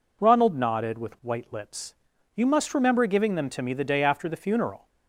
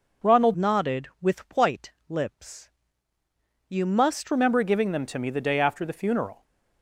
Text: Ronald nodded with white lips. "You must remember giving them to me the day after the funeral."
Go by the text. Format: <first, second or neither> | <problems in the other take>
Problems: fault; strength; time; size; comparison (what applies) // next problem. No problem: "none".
first | changes voice from "nodded" to "must"; from 0.5 to 4.3 s; 3.8 s long // pauses between "white" and "lips"; slight; at 1.9 s; 0.18 s long